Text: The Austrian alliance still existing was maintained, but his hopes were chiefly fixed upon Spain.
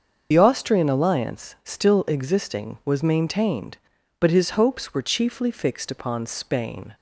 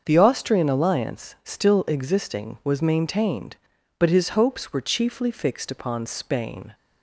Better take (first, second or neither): second